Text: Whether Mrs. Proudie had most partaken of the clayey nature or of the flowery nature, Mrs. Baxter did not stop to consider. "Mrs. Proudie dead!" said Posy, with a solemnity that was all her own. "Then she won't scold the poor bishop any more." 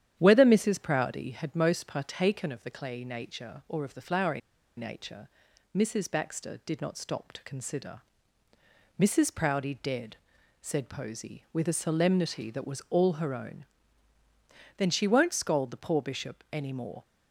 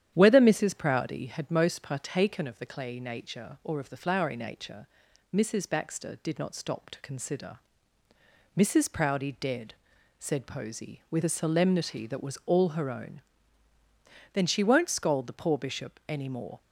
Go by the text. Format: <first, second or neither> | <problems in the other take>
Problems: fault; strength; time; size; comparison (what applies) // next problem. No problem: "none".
second | starts louder than the rest; strong; until 1.1 s; 10 dB; strong in the second // pauses between "flowery" and "nature"; at 4.4 s; 0.37 s long